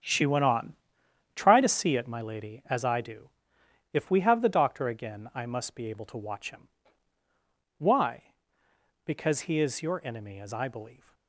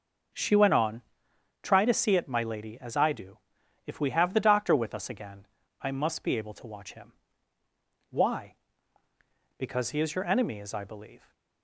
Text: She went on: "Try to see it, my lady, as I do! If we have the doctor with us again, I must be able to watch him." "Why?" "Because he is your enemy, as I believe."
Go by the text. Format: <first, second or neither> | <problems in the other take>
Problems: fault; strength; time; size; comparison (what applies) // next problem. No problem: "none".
second | starts louder than the rest; strong; until 1.6 s; 8.5 dB // skips "with us"; at 4.8 s